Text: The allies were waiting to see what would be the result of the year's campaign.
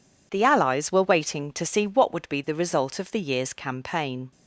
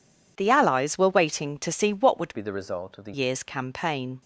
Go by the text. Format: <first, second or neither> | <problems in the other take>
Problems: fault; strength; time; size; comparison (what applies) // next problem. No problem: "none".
first | changes voice from "be" to "the"; from 2.3 to 3.1 s; 0.8 s long